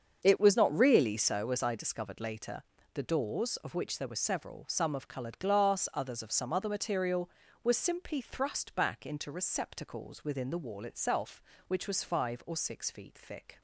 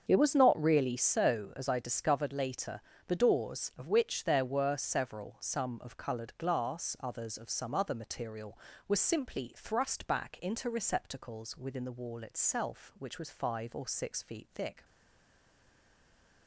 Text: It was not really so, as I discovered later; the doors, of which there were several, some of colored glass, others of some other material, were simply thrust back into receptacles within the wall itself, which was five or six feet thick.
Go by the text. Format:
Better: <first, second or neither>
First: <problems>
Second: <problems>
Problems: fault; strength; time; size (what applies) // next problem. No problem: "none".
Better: first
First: starts louder than the rest; until 1.2 s; 7 dB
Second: starts louder than the rest; strong; until 1.0 s; 7 dB // stays silent after the last word; noticeable; from 14.8 s on; 1.6 s long